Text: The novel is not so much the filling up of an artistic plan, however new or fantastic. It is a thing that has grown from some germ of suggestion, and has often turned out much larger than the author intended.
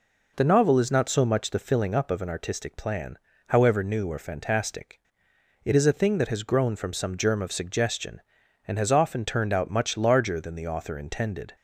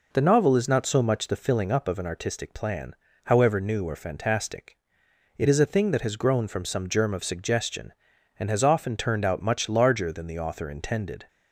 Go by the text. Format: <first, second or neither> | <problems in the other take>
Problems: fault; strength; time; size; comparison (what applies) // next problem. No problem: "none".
neither | none